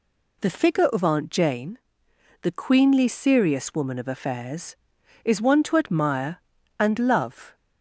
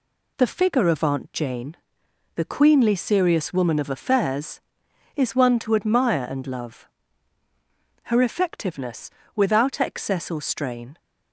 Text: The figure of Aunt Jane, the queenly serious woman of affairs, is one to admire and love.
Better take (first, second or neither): first